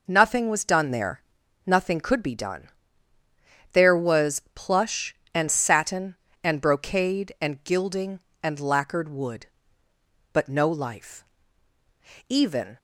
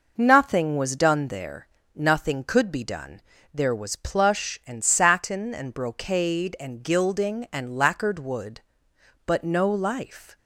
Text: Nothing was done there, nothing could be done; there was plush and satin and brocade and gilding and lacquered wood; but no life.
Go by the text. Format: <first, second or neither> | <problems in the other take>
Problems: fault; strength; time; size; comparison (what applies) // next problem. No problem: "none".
second | goes on to say "Even"; slight; from 12.2 s on; 0.48 s long